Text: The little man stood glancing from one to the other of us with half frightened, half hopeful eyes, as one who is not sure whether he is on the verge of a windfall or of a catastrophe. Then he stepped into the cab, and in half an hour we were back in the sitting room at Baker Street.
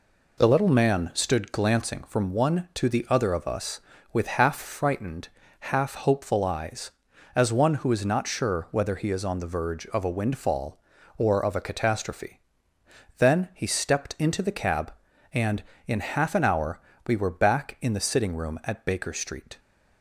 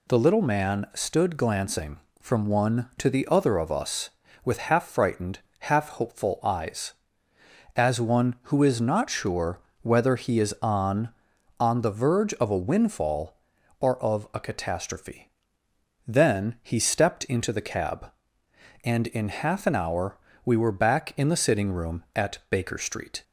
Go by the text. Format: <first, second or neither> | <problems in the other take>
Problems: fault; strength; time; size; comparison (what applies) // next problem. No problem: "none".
first | pauses between "sure" and "whether"; slight; at 9.5 s; 0.22 s long // says "on" twice; at 11.5 s // pauses between "hour" and "we"; slight; at 20.1 s; 0.28 s long; slight in the first